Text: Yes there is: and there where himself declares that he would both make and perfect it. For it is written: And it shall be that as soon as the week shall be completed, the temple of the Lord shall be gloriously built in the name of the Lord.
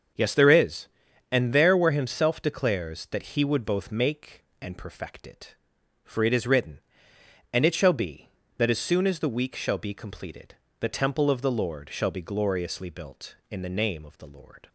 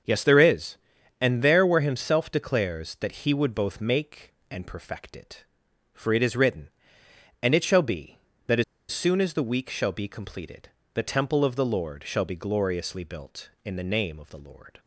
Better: first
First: starts louder than the rest; until 1.6 s; 7 dB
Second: starts louder than the rest; until 1.4 s; 7 dB // pauses between "as" and "soon"; slight; at 8.6 s; 0.27 s long

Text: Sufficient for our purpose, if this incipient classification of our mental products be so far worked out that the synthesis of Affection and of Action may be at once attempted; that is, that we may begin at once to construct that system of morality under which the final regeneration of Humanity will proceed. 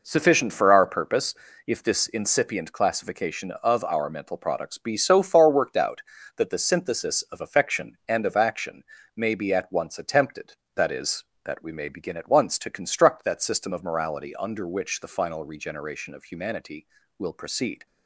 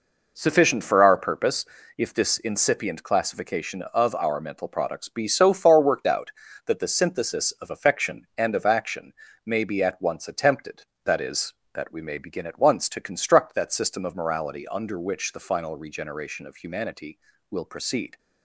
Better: neither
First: pauses between "Action" and "may"; slight; at 8.8 s; 0.32 s long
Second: pauses between "Action" and "may"; slight; at 9.1 s; 0.32 s long

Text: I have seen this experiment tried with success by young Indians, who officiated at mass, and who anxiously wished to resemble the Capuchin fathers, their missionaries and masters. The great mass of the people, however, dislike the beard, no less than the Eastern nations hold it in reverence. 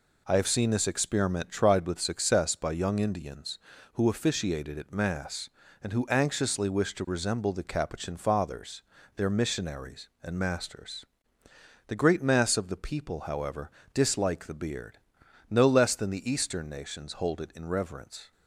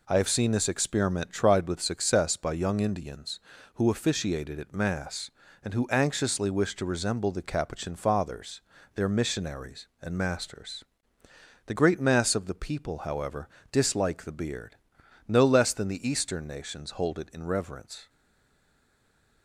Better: first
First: none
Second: stays silent after the last word; noticeable; from 18.0 s on; 1.4 s long

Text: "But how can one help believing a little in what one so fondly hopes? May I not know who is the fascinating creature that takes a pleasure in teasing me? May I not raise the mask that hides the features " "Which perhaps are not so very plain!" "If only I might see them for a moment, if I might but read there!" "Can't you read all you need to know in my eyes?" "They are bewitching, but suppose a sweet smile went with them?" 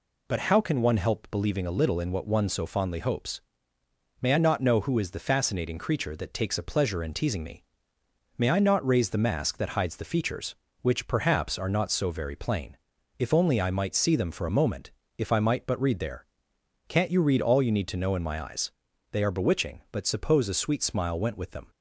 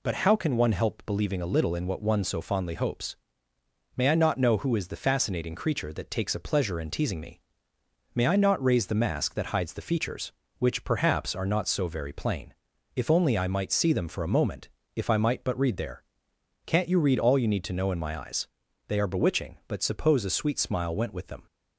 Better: neither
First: none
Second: none

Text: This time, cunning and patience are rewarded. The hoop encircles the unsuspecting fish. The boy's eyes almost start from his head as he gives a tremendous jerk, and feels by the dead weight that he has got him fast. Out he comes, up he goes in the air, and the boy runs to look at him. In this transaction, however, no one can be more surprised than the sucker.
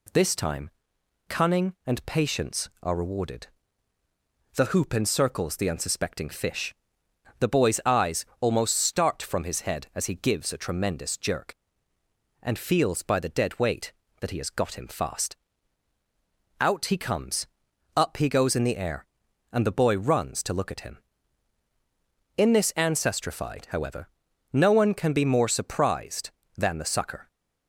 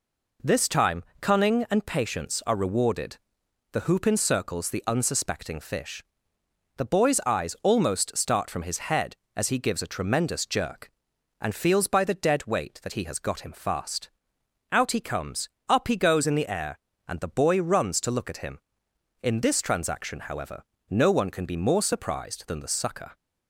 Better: second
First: says "ancestrified" for "transaction"; at 22.7 s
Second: none

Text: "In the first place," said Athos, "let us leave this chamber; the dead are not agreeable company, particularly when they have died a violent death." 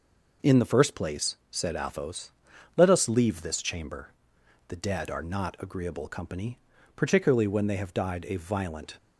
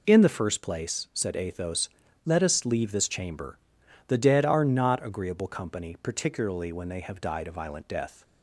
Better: second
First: stops before "death"; at 8.9 s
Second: none

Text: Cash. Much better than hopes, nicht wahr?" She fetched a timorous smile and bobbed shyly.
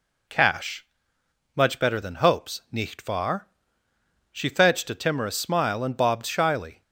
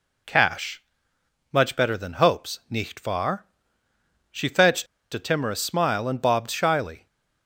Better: first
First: none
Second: pauses between "fetched" and "a"; slight; at 4.8 s; 0.27 s long

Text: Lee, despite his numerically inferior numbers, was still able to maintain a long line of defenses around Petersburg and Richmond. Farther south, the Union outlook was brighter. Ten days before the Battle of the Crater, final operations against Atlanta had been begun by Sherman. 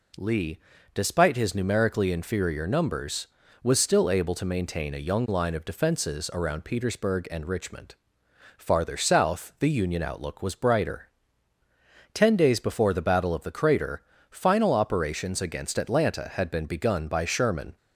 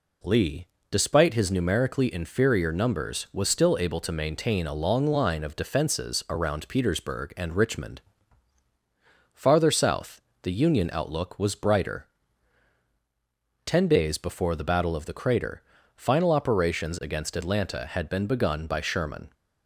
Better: second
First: says "young" for "long"; at 5.0 s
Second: none

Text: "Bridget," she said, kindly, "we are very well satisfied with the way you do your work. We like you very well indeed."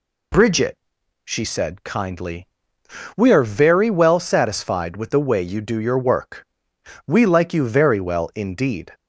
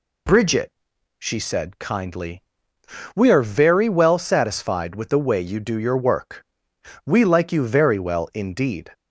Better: neither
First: none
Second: none

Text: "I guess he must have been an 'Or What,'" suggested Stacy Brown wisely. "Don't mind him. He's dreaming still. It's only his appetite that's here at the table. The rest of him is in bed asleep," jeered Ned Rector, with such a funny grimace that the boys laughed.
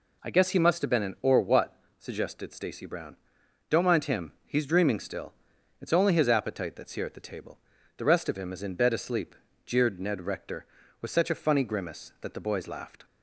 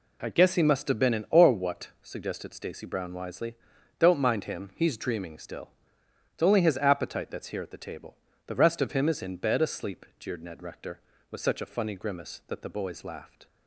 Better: second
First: skips "wisely"; at 3.4 s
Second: none

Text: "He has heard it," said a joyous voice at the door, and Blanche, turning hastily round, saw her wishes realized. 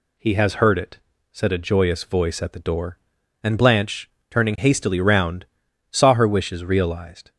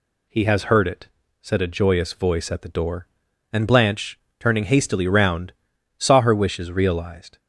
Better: neither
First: none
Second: none

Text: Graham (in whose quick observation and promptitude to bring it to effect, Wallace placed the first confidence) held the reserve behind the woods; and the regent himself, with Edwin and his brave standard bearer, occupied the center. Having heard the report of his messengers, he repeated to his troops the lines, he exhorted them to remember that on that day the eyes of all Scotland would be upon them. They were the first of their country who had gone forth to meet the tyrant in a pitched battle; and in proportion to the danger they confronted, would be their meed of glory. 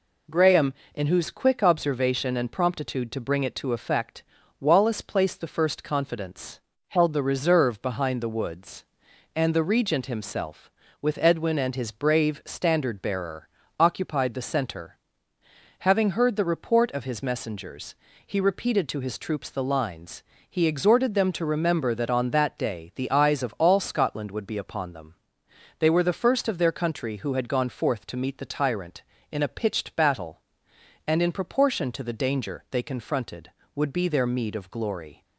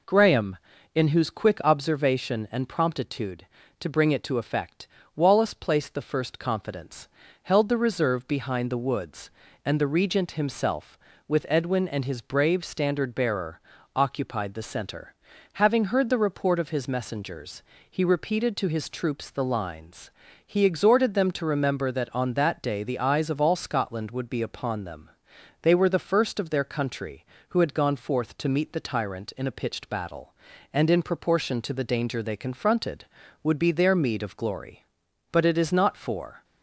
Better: first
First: none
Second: goes on to say "But it is not for"; noticeable; from 35.2 s on; 1.1 s long

